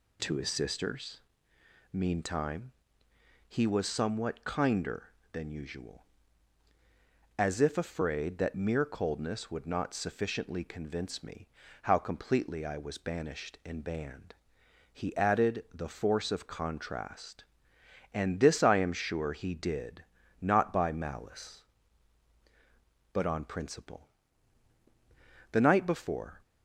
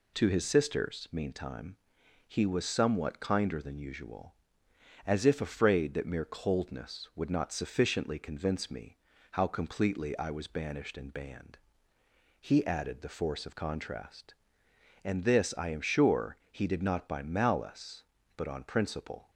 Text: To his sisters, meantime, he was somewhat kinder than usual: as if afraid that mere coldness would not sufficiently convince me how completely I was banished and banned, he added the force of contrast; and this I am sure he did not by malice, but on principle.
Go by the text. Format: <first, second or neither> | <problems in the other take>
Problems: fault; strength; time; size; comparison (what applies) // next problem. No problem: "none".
second | pauses between "me" and "how"; slight; at 11.4 s; 0.34 s long; slight in the second // pauses between "did" and "not"; slight; at 20.0 s; 0.36 s long // goes on to say "The night before"; noticeable; from 25.5 s on; 0.88 s long